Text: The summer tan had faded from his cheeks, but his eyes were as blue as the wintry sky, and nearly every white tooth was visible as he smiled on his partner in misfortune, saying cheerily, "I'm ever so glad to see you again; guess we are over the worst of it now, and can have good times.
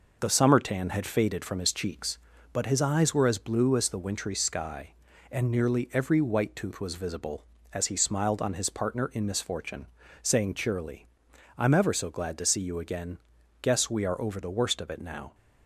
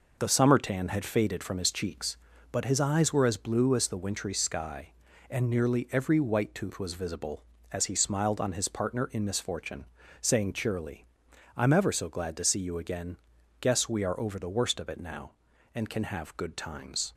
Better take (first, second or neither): second